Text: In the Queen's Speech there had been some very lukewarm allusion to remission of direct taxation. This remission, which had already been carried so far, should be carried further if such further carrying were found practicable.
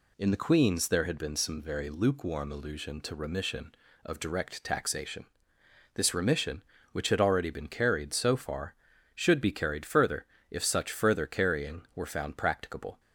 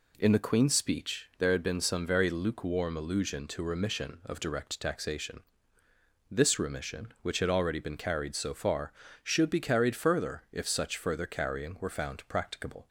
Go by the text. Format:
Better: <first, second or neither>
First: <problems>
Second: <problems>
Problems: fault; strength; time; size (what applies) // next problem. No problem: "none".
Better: second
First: skips "Speech"; at 0.8 s // pauses between "further" and "if"; slight; at 10.2 s; 0.26 s long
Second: none